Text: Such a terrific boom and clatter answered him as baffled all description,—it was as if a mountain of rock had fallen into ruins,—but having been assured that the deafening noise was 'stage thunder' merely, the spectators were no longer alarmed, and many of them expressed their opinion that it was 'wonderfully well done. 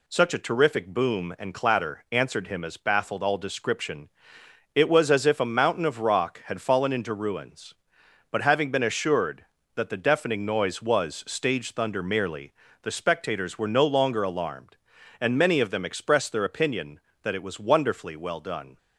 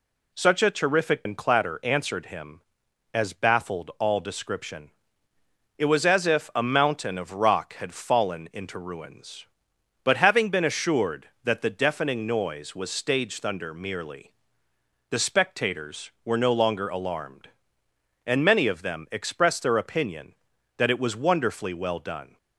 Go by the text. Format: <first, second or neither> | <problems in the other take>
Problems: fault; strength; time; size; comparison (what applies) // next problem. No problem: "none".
first | skips "boom"; at 1.2 s